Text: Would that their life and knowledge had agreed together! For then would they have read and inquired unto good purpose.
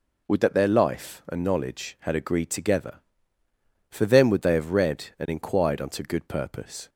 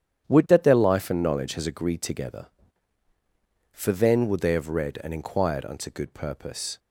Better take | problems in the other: first | starts louder than the rest; strong; until 1.2 s; 10 dB // says "has" for "had"; at 1.5 s

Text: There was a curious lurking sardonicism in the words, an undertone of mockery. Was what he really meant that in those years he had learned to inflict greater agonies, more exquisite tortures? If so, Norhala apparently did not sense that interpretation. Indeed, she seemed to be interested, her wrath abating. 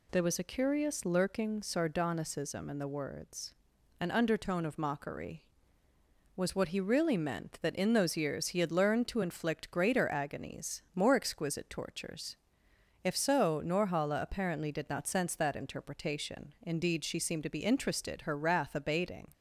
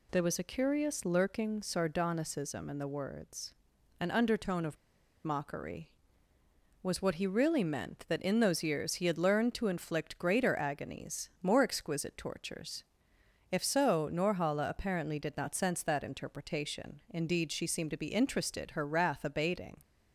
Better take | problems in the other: first | pauses between "of" and "mockery"; noticeable; at 4.7 s; 0.47 s long

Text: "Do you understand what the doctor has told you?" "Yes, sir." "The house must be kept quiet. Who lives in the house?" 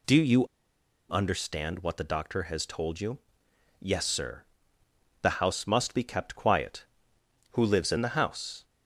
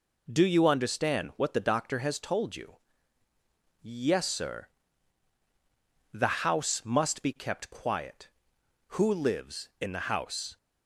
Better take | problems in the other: second | pauses between "you" and "understand"; noticeable; at 0.4 s; 0.68 s long

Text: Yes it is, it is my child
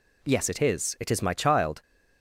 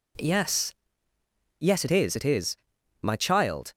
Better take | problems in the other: first | says "Yes" twice; at 1.5 s // pauses between "is" and "my"; at 2.5 s; 0.44 s long

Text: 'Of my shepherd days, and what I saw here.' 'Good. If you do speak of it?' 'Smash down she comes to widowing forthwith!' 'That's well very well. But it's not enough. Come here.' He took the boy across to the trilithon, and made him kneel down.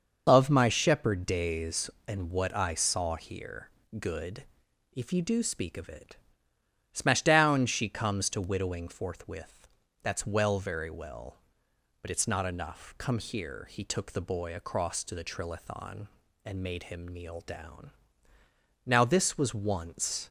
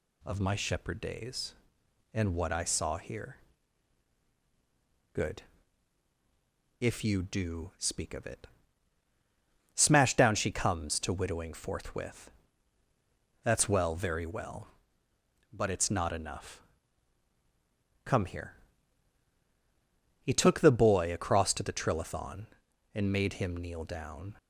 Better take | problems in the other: second | starts louder than the rest; until 1.2 s; 6.5 dB // goes on to say "Now this was once"; from 18.8 s on; 1.4 s long

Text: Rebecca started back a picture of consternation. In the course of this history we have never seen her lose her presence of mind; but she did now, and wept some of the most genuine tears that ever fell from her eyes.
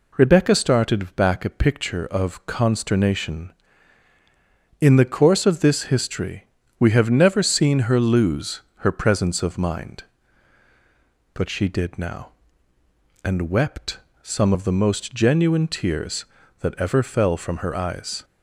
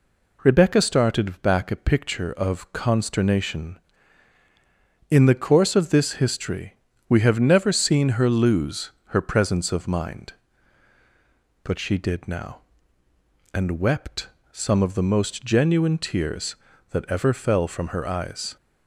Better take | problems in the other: neither | pauses between "history" and "we"; slight; the same in both // pauses between "lose" and "her"; slight; the same in both // pauses between "wept" and "some"; slight; the same in both

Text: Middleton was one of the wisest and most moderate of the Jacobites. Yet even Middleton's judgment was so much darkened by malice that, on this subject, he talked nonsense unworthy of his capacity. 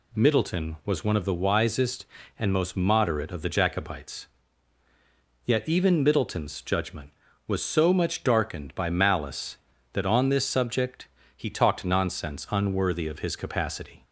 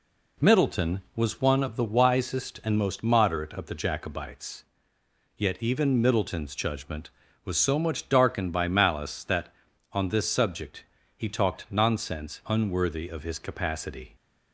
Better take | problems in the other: neither | none

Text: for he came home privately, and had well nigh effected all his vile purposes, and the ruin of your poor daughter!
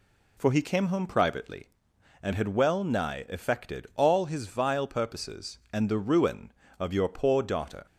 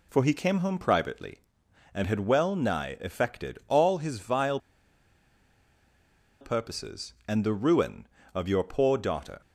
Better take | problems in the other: first | pauses between "vile" and "purposes"; strong; at 4.5 s; 1.8 s long

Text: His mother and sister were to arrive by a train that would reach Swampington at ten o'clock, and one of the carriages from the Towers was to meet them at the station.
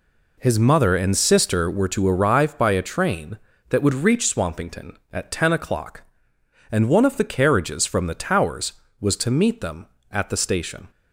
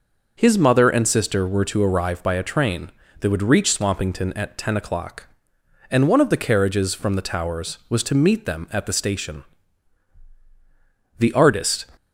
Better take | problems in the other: first | goes on to say "The artist"; noticeable; from 11.1 s on; 0.70 s long

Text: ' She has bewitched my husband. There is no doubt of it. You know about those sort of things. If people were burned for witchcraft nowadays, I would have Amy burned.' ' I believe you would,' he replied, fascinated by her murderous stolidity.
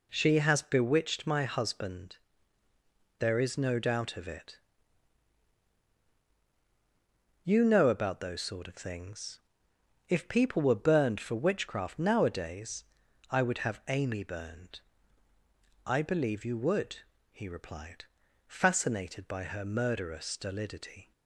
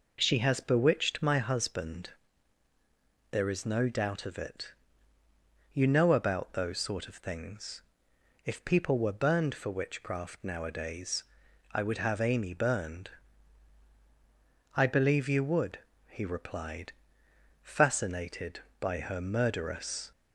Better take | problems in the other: first | stops before "stolidity"; at 20.1 s

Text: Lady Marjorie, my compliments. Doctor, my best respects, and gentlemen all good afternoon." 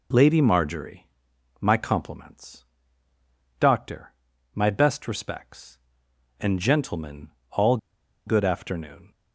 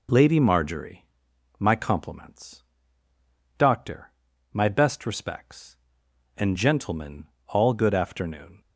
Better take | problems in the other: second | pauses between "gentlemen" and "all"; slight; at 7.2 s; 0.22 s long; slight in the second // pauses between "all" and "good"; noticeable; at 7.7 s; 0.49 s long

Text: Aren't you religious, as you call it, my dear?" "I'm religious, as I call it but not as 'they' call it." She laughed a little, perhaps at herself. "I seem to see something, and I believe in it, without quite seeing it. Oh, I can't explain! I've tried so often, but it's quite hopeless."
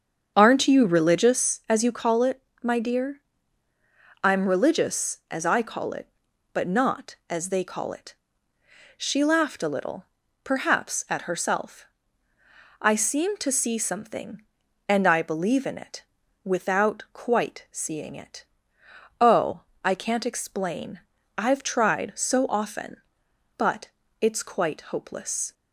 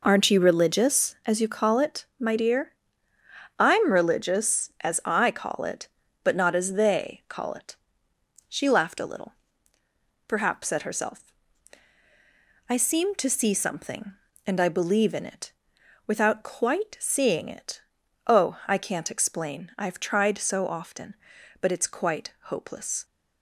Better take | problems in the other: second | starts louder than the rest; until 1.5 s; 7 dB // pauses between "but" and "it's"; slight; at 23.8 s; 0.34 s long

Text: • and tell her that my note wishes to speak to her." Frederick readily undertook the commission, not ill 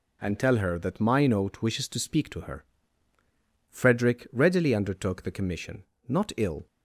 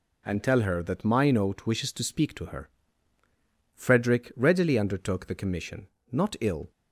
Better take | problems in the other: neither | none

